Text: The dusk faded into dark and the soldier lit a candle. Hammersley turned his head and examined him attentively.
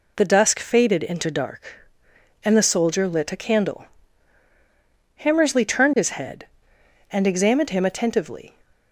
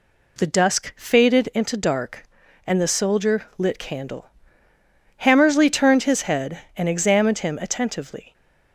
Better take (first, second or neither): first